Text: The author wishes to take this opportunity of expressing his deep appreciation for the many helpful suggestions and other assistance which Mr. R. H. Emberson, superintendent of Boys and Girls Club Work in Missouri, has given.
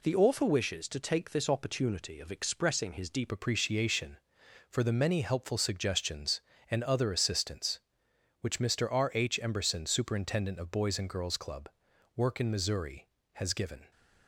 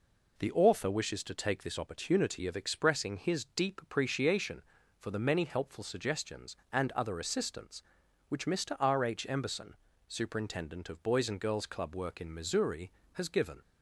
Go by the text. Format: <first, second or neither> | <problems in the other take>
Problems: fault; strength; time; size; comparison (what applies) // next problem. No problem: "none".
second | changes voice at "appreciation"; from 3.3 s on; 10.6 s long // pauses between "Club" and "Work"; noticeable; at 11.7 s; 0.46 s long